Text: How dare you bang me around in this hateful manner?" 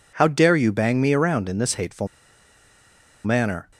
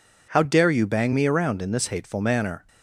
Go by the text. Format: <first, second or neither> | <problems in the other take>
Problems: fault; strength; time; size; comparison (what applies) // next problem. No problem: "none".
second | pauses between "hateful" and "manner"; at 2.0 s; 1.1 s long